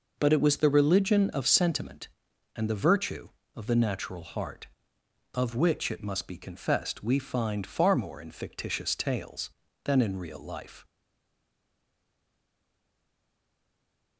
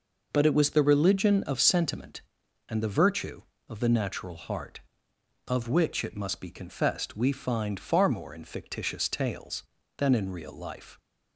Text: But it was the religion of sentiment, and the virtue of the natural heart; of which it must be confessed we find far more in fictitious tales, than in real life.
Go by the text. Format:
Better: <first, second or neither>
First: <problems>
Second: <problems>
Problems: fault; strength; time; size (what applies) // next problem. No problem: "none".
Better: second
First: stays silent after the last word; strong; from 10.8 s on; 3.3 s long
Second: none